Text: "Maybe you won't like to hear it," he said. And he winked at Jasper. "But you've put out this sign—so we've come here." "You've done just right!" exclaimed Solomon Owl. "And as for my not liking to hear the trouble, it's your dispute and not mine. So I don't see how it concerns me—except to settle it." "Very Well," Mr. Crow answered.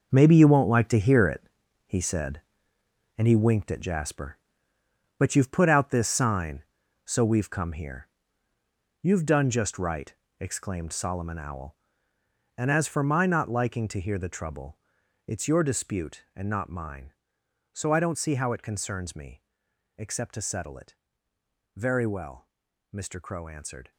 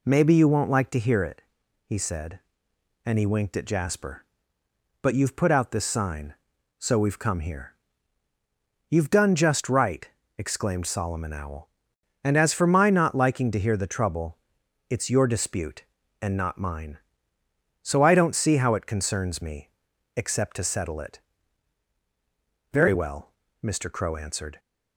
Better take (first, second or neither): second